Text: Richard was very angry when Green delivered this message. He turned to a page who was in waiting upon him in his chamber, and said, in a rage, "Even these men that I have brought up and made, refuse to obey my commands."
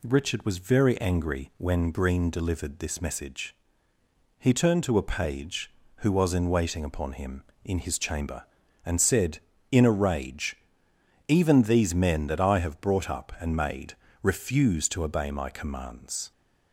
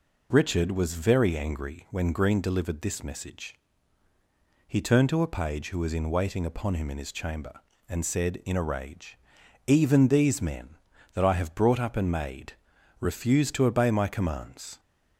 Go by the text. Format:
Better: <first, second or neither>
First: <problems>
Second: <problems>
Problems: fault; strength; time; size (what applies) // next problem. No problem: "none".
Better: neither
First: none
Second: none